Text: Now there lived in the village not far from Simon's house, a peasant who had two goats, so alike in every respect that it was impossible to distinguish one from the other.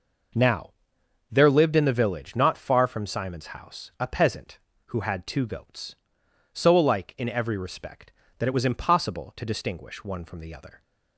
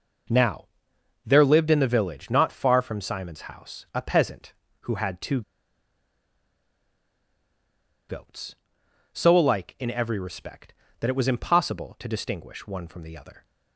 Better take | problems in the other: first | pauses between "Now" and "there"; noticeable; at 0.6 s; 0.60 s long; noticeable in the first // pauses between "two" and "goats"; strong; at 5.4 s; 2.6 s long

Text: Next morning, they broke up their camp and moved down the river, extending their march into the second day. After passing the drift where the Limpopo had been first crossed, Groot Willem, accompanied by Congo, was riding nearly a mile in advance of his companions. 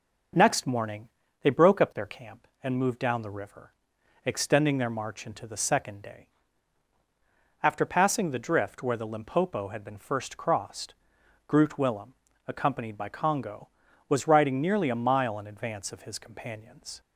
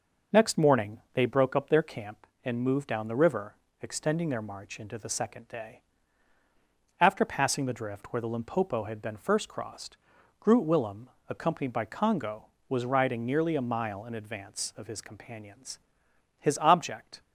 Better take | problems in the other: first | goes on to say "His object"; noticeable; from 16.3 s on; 0.82 s long

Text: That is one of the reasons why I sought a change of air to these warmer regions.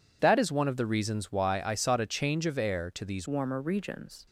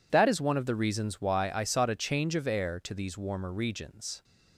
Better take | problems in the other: second | changes voice at "warmer"; from 3.2 s on; 1.0 s long

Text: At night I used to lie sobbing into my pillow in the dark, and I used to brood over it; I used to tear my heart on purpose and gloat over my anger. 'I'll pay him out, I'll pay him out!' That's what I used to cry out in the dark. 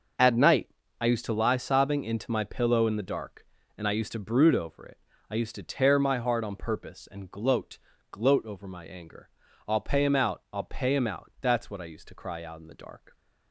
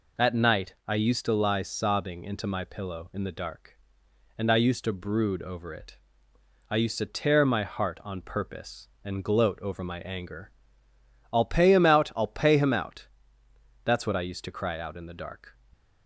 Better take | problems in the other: second | starts louder than the rest; until 1.5 s; 6.5 dB // pauses between "night" and "I"; slight; at 0.6 s; 0.32 s long // says "gloat" twice; at 8.1 s

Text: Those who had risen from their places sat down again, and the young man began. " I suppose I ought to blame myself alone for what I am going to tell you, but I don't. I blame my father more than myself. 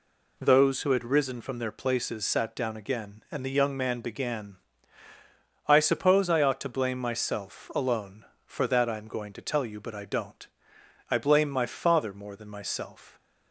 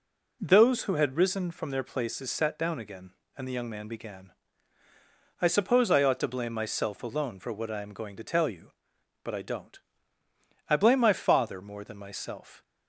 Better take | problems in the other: second | says "that" for "what"; at 8.6 s

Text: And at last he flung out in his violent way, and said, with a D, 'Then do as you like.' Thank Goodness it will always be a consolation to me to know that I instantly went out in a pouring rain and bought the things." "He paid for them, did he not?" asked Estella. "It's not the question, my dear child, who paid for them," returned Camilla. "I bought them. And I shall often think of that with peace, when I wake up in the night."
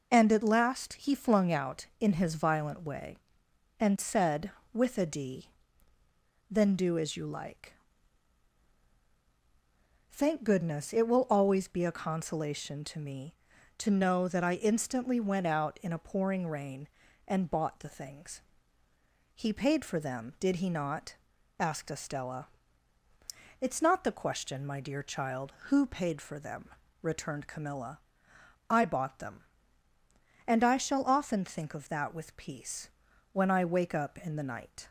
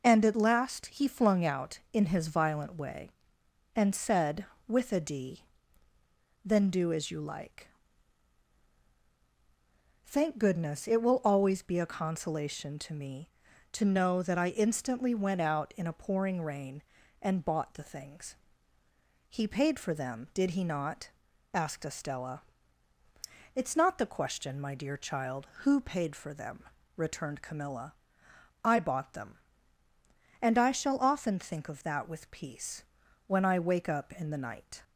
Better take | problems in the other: neither | none

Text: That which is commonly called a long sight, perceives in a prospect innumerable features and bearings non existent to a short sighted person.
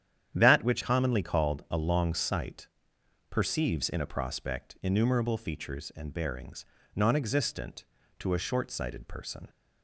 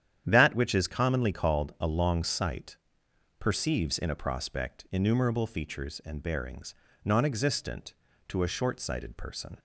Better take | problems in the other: second | starts louder than the rest; strong; until 1.3 s; 9.5 dB; strong in the second // skips "is"; at 0.8 s // pauses between "bearings" and "non"; slight; at 6.6 s; 0.32 s long; slight in the second

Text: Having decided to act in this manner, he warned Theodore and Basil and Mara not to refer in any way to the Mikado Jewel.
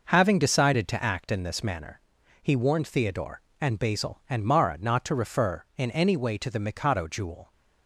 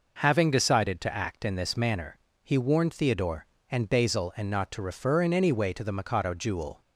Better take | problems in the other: first | skips "Mara"; at 4.4 s

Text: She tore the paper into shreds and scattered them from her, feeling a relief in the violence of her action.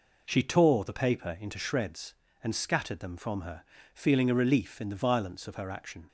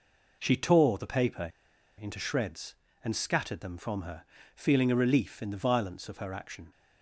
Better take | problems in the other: first | pauses between "paper" and "into"; noticeable; at 1.5 s; 0.49 s long

